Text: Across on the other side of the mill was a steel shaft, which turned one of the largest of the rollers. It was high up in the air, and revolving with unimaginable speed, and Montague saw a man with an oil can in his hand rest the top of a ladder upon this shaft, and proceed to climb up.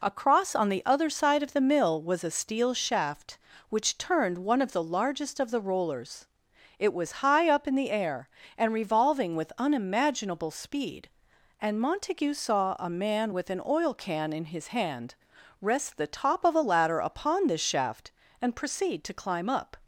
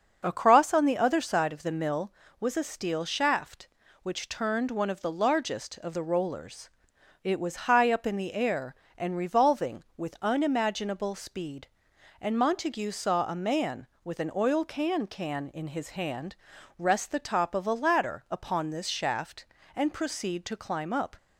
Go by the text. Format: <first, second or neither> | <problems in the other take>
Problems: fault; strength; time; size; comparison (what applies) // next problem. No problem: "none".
first | starts louder than the rest; until 1.2 s; 6.5 dB // says "can" twice; at 15.0 s // pauses between "hand" and "rest"; at 16.3 s; 0.42 s long; noticeable in the first